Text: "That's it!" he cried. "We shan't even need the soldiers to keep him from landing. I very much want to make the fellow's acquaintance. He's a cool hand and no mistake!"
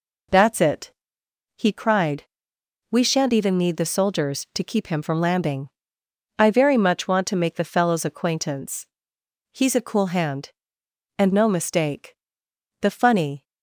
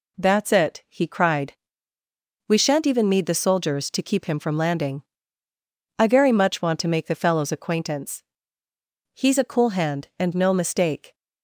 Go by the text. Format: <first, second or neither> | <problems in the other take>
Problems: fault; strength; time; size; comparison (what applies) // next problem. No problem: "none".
second | goes on to say "The funny"; noticeable; from 12.8 s on; 0.62 s long